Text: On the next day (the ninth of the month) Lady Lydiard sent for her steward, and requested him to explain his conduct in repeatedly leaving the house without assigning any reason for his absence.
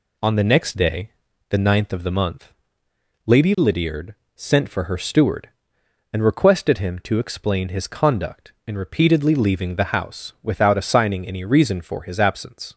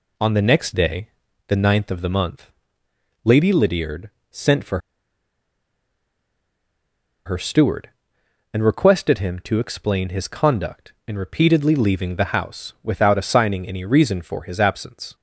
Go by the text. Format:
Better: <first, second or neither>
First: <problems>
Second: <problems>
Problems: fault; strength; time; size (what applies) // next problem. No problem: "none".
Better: first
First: pauses between "Lydiard" and "sent"; slight; at 4.1 s; 0.24 s long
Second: pauses between "Lydiard" and "sent"; slight; at 4.0 s; 0.24 s long // pauses between "for" and "her"; strong; at 4.7 s; 2.4 s long